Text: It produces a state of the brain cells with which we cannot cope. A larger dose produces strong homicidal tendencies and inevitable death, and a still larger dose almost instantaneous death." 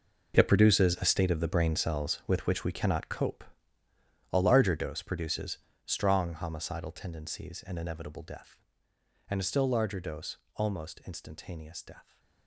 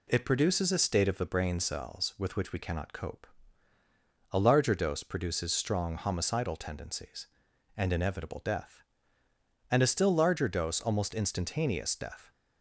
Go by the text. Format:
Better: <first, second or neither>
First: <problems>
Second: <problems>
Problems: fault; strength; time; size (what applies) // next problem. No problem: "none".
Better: second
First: gets quieter; strong; throughout; 14.5 dB // pauses between "produces" and "strong"; slight; at 5.5 s; 0.26 s long // pauses between "dose" and "almost"; slight; at 10.3 s; 0.22 s long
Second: none